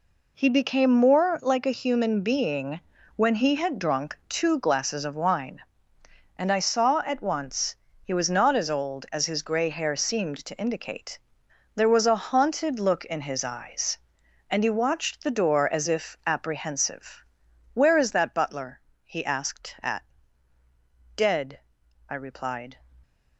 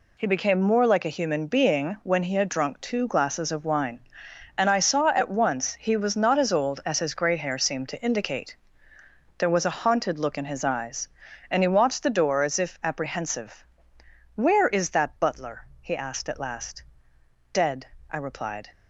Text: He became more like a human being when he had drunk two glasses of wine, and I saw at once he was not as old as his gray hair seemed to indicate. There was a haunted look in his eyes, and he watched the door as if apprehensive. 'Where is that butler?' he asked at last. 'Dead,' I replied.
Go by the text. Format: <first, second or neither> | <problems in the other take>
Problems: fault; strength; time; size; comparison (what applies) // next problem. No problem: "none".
second | pauses between "being" and "when"; slight; at 2.8 s; 0.34 s long // pauses between "once" and "he"; slight; at 7.7 s; 0.26 s long // skips "last"; at 20.5 s